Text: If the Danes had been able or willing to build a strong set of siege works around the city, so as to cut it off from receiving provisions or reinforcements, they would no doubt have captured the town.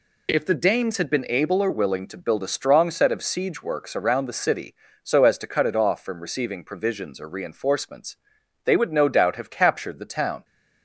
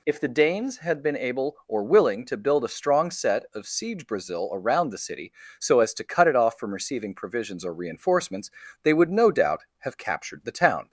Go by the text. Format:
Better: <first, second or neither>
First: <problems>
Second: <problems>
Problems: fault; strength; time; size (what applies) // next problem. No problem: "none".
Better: first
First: none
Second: says "brazil" for "works"; at 4.0 s